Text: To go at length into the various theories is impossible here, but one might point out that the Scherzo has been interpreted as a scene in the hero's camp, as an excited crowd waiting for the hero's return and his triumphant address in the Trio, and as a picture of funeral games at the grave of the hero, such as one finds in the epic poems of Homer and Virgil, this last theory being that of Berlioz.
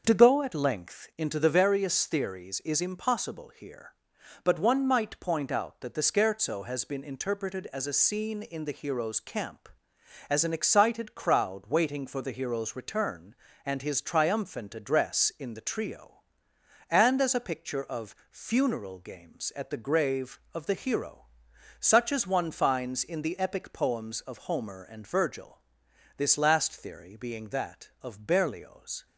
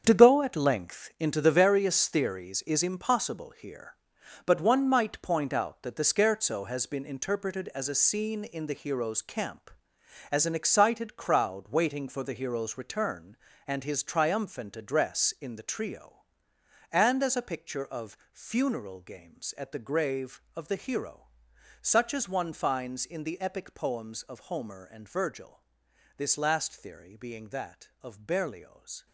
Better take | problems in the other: first | gets quieter; strong; throughout; 12 dB // starts louder than the rest; strong; until 1.0 s; 7.5 dB; also in the first // pauses between "of" and "funeral"; slight; at 18.1 s; 0.16 s long; slight in the first

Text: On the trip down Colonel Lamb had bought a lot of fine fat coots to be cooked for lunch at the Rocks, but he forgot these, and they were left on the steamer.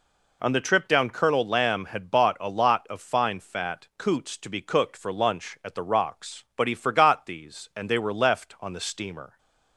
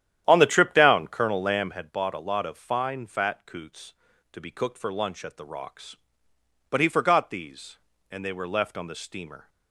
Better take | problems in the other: first | starts louder than the rest; strong; until 1.9 s; 10.5 dB

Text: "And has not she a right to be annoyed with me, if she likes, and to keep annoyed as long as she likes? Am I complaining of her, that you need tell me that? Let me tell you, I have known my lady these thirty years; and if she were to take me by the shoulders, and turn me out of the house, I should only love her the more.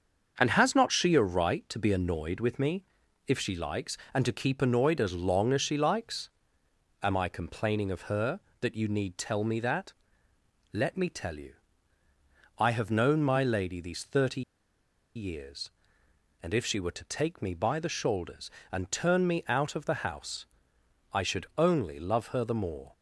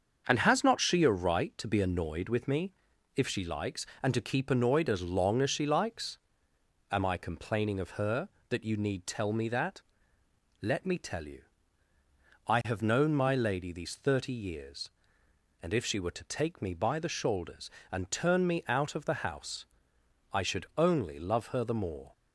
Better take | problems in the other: second | starts louder than the rest; until 1.3 s; 7 dB; also in the second // pauses between "thirty" and "years"; noticeable; at 14.4 s; 0.74 s long

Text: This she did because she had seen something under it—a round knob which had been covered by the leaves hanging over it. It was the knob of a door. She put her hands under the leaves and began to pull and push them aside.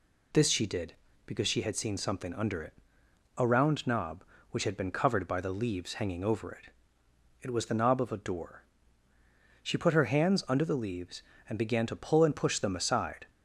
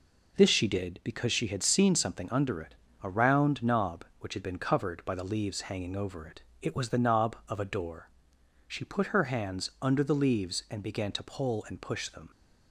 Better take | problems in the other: first | stops before "aside"; at 12.3 s

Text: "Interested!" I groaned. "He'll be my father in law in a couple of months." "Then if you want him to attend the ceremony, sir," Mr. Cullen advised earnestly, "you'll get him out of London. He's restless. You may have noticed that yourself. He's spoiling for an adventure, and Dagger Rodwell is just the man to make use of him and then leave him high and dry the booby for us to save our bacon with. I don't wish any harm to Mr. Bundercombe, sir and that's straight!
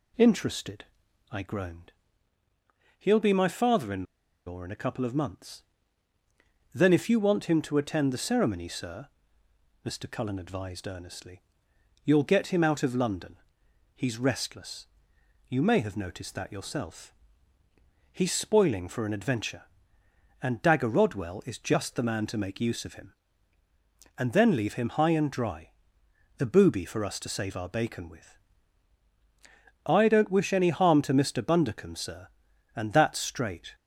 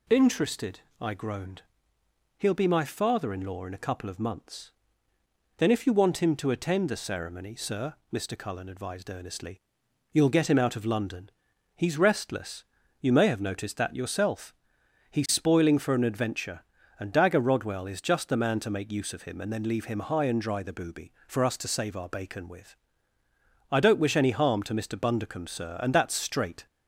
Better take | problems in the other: second | pauses between "in" and "law"; at 4.0 s; 0.42 s long // pauses between "dry" and "the"; noticeable; at 25.7 s; 0.64 s long

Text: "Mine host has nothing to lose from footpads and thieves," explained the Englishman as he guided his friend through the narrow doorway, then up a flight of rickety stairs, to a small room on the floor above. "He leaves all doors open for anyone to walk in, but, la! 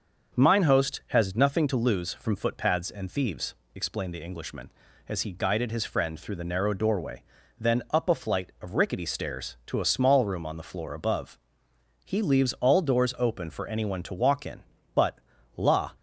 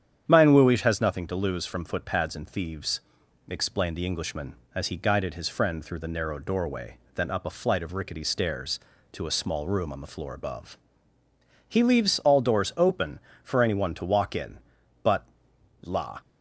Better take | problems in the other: first | starts louder than the rest; strong; until 1.2 s; 9 dB; also in the first // says "wuish" for "host"; at 0.5 s

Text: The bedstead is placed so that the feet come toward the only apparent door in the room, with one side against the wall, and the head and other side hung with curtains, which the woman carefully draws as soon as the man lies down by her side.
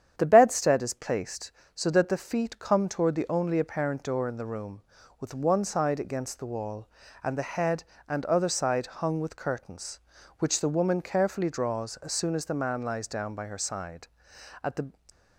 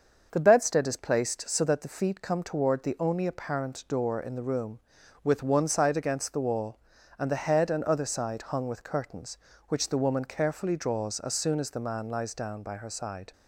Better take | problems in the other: second | starts louder than the rest; strong; until 1.1 s; 9 dB; also in the second // goes on to say "At the"; slight; from 14.6 s on; 0.26 s long

